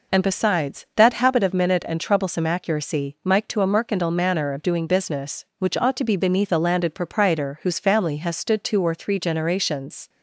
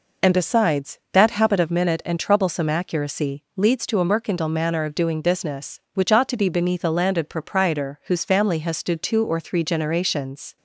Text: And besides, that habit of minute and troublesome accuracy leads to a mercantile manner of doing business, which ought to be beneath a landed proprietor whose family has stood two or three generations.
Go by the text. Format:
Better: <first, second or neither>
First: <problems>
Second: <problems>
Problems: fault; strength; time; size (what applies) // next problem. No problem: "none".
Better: second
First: says "mike" for "leads"; at 3.2 s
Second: none